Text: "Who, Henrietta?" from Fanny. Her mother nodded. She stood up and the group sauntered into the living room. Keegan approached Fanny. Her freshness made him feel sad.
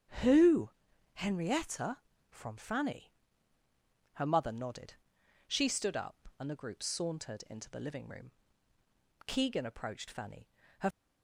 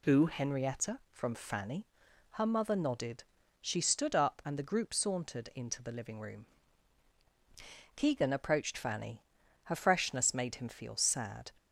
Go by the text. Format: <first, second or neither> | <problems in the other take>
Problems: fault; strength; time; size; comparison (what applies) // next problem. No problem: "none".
second | starts louder than the rest; strong; until 1.6 s; 8 dB // stops before "freshness made him feel sad"; at 10.9 s